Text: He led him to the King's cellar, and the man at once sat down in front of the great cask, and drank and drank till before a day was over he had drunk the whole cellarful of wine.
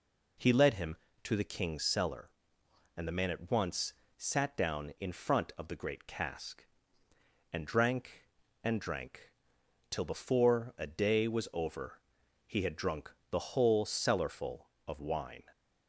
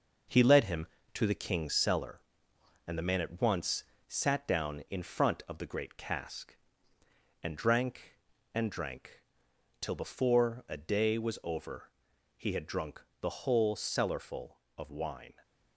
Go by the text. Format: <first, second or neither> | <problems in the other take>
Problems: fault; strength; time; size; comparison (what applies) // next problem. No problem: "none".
first | gets quieter; noticeable; throughout; 5.5 dB // pauses between "once" and "sat"; slight; at 3.8 s; 0.24 s long; slight in the first // pauses between "drank" and "till"; noticeable; at 9.2 s; 0.58 s long; noticeable in the first // pauses between "over" and "he"; noticeable; at 11.8 s; 0.46 s long; noticeable in the first // pauses between "drunk" and "the"; slight; at 13.0 s; 0.18 s long; slight in the first